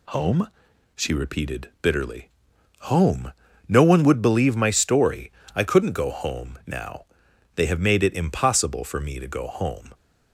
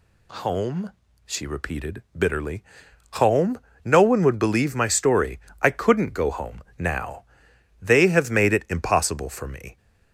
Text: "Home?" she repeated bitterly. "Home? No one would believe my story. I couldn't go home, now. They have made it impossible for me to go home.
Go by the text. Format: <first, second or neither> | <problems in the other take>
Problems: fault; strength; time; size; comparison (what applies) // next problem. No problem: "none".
first | stops before "to go home"; at 9.7 s